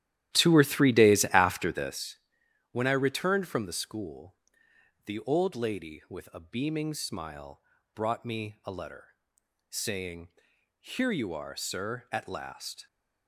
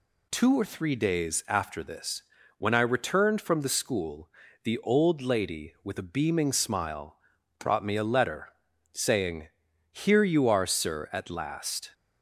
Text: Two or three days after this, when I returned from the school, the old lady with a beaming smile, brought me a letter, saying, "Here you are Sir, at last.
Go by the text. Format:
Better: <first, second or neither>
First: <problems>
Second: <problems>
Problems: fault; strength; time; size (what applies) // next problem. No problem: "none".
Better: second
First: starts louder than the rest; strong; until 2.1 s; 12.5 dB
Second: none